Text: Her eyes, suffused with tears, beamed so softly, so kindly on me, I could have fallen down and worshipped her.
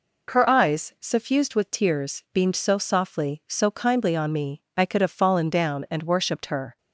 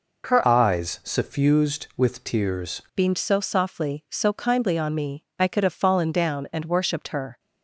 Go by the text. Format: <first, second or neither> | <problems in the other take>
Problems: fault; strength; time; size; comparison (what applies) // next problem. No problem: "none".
first | changes voice from "eyes" to "tears"; from 0.4 to 2.8 s; 2.4 s long